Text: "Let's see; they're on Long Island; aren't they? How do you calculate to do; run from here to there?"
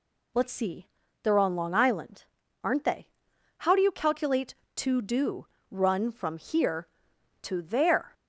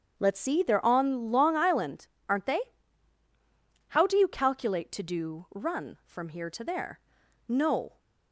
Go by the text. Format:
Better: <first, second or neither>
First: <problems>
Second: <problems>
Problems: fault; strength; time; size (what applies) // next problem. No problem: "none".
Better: first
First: none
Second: starts louder than the rest; strong; until 1.1 s; 7.5 dB // goes on to say "No"; from 7.4 s on; 0.52 s long